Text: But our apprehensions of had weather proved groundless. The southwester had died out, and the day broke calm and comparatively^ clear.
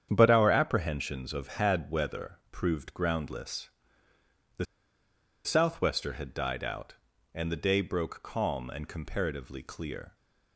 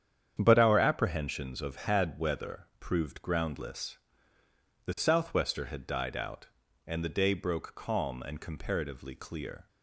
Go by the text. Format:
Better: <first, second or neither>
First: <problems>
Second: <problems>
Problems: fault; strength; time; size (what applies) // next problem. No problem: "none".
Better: second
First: starts louder than the rest; strong; until 1.1 s; 8.5 dB // pauses between "The" and "southwester"; noticeable; at 4.6 s; 0.79 s long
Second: starts louder than the rest; strong; until 1.4 s; 8.5 dB